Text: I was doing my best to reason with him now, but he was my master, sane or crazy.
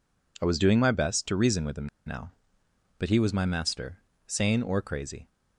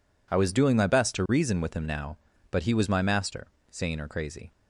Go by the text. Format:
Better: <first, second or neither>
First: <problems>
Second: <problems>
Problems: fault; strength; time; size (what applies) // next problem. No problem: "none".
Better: second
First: pauses between "him" and "now"; slight; at 1.8 s; 0.17 s long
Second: none